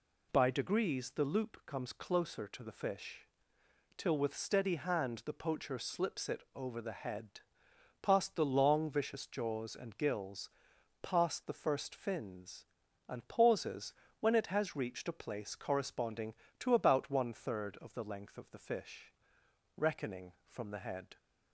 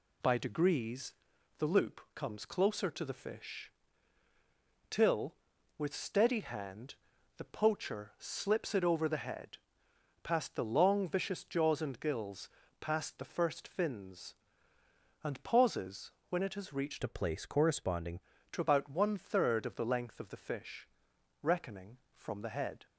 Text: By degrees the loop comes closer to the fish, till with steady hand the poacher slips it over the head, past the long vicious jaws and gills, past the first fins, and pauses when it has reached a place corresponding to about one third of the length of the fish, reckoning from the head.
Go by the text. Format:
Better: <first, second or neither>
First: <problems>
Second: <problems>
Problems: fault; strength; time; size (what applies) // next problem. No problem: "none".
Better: first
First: pauses between "pauses" and "when"; slight; at 13.9 s; 0.28 s long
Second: pauses between "degrees" and "the"; at 1.1 s; 0.44 s long // pauses between "hand" and "the"; at 6.9 s; 0.44 s long // pauses between "pauses" and "when"; slight; at 16.1 s; 0.18 s long // changes voice from "a" to "corresponding"; from 17.0 to 18.1 s; 1.1 s long